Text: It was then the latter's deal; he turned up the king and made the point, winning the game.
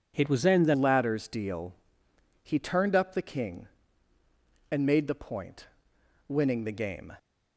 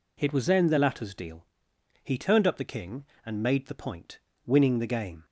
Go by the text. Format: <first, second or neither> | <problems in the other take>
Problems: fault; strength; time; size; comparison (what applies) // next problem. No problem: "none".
second | changes voice at "latter's"; from 0.7 s on; 6.4 s long